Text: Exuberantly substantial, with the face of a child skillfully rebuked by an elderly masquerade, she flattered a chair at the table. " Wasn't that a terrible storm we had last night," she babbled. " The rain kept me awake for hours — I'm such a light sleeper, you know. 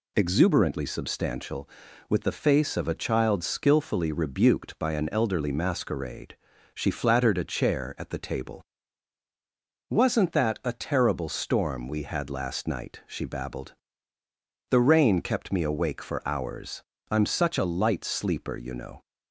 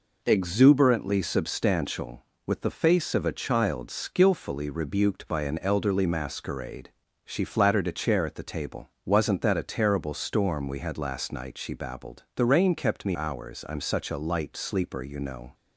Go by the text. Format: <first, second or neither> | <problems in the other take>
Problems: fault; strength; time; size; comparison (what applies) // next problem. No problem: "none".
first | skips "awake for"; at 13.1 s